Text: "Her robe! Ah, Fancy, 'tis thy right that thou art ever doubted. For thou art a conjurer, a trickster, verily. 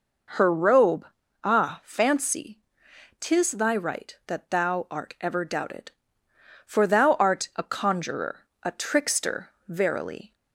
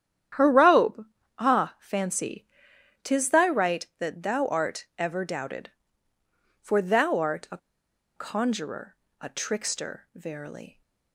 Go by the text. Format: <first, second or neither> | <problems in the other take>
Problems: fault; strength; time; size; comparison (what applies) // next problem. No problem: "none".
first | starts louder than the rest; strong; until 1.7 s; 10 dB // pauses between "a" and "conjurer"; noticeable; at 7.5 s; 0.58 s long